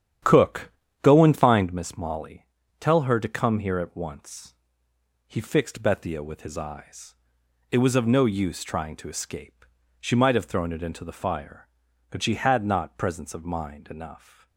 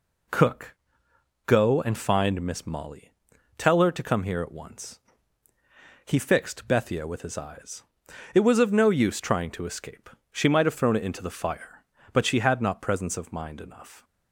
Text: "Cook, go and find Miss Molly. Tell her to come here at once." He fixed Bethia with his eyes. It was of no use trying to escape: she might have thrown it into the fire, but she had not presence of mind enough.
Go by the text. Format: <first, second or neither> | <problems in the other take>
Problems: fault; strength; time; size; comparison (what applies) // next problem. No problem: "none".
second | starts louder than the rest; strong; until 1.9 s; 9.5 dB